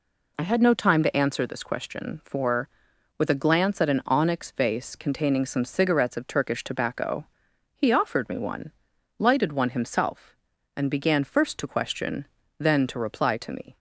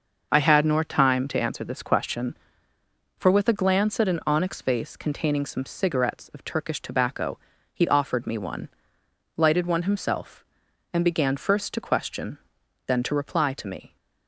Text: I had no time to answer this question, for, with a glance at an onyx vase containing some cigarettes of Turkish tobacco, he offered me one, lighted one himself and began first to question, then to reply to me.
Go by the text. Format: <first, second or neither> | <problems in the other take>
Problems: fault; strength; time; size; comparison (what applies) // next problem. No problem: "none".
first | says "nor" for "no"; at 0.6 s